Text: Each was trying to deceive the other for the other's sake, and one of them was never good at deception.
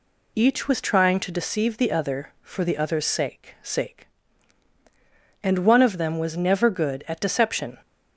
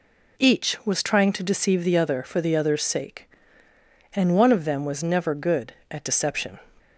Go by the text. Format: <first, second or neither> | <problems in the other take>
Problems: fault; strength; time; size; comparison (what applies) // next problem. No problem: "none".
second | says "sake" twice; at 3.6 s